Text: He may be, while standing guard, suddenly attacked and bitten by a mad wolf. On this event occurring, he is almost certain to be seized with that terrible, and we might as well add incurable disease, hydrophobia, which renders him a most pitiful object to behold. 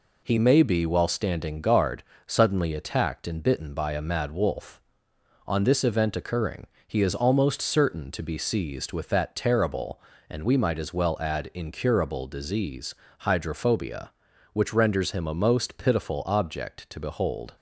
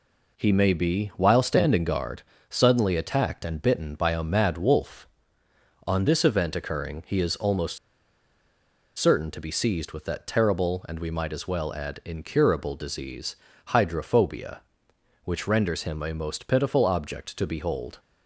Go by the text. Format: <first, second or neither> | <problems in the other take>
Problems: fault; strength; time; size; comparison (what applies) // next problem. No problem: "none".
first | pauses between "almost" and "certain"; at 7.7 s; 1.2 s long